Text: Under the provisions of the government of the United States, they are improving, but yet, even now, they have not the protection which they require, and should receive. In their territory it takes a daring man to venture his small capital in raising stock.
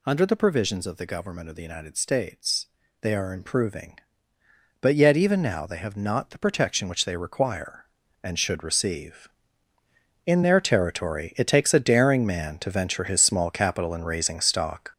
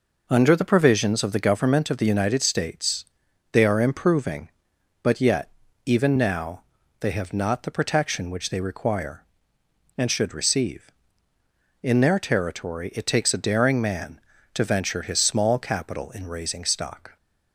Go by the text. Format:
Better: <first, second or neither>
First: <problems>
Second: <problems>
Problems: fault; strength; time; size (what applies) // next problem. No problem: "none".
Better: second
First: gets louder; strong; throughout; 7 dB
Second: none